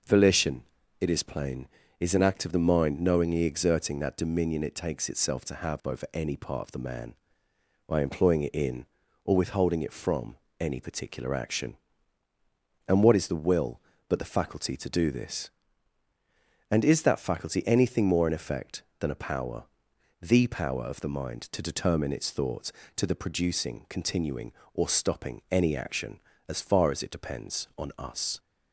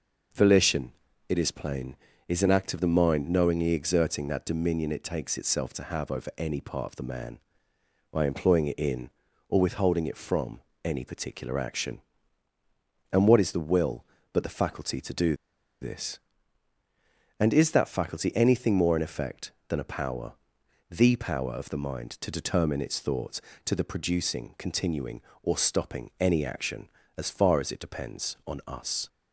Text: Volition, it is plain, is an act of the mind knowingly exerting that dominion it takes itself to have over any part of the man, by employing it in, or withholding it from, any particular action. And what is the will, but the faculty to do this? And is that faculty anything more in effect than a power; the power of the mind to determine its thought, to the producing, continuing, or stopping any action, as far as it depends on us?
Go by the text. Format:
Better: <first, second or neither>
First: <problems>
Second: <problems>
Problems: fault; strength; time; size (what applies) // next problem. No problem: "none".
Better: first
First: none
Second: pauses between "do" and "this"; noticeable; at 15.3 s; 0.46 s long